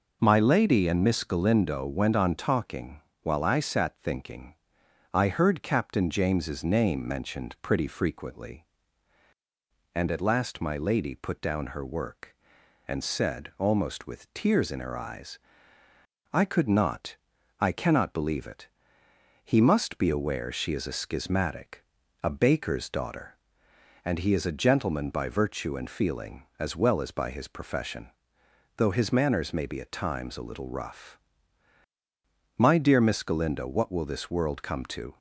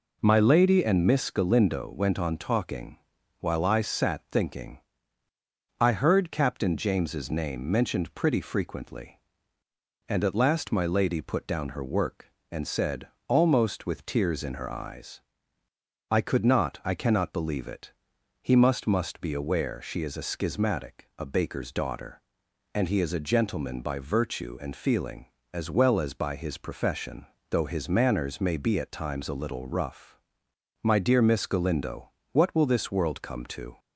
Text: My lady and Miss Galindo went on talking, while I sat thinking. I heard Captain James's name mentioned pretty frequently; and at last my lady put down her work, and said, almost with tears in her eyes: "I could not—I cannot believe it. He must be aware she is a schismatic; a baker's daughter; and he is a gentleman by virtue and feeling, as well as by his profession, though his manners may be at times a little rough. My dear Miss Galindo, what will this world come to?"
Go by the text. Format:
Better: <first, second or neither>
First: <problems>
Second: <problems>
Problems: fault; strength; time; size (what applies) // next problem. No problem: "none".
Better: first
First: none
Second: says "must" twice; at 18.8 s